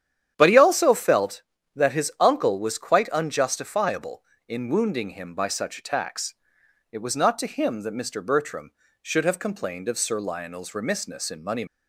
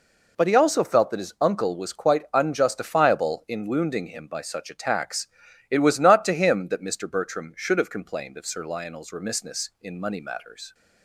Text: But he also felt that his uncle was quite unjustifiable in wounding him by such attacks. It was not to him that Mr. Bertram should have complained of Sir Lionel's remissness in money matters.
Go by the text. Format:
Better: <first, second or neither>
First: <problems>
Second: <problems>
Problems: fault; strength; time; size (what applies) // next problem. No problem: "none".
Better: second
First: starts louder than the rest; strong; until 1.3 s; 10 dB // stops before "matters"; at 11.6 s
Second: none